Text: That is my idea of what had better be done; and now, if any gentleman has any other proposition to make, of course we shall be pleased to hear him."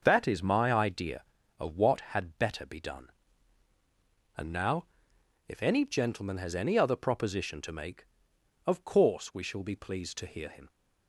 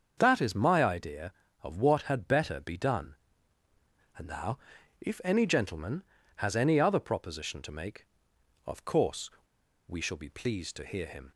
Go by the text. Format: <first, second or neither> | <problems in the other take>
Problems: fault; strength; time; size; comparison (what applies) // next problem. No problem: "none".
first | starts louder than the rest; until 1.1 s; 7 dB; noticeable in the first // pauses between "course" and "we"; noticeable; at 9.3 s; 0.56 s long